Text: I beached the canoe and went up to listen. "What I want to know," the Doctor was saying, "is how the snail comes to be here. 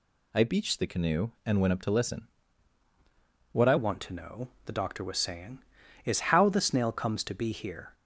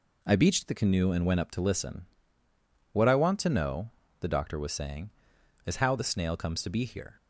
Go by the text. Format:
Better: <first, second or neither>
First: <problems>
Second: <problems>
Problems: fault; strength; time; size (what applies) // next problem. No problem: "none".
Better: second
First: changes voice at "want"; from 3.7 s on; 4.2 s long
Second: none